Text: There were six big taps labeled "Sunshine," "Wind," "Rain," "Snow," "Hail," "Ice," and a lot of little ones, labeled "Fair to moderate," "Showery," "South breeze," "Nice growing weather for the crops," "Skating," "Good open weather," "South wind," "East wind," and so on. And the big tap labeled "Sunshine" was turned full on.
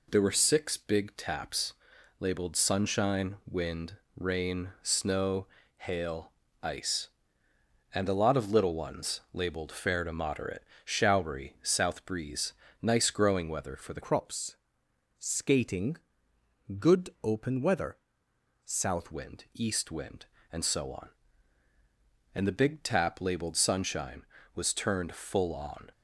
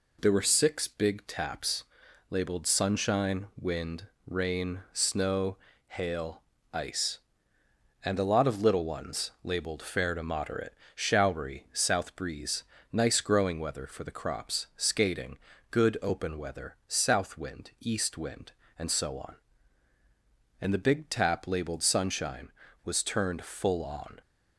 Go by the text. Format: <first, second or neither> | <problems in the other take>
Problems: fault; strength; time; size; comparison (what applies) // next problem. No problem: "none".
second | pauses between "taps" and "labeled"; noticeable; at 1.7 s; 0.46 s long; noticeable in the second // changes voice from "crops" to "South"; from 14.0 to 19.1 s; 5.1 s long // pauses between "Good" and "open"; slight; at 17.0 s; 0.16 s long